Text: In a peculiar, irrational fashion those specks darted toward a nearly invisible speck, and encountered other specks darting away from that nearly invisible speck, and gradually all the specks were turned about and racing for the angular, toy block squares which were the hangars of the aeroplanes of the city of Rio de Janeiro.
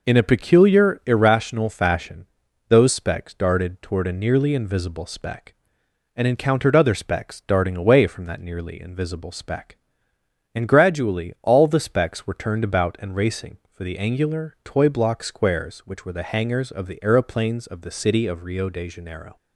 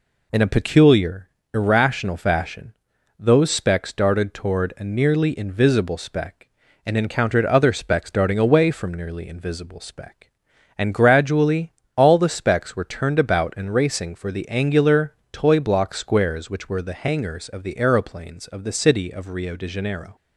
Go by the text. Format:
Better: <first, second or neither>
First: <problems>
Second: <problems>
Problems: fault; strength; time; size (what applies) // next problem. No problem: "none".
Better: first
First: pauses between "fashion" and "those"; at 2.2 s; 0.44 s long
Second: pauses between "fashion" and "those"; noticeable; at 2.7 s; 0.48 s long // skips "that"; at 8.9 s // pauses between "gradually" and "all"; slight; at 11.7 s; 0.24 s long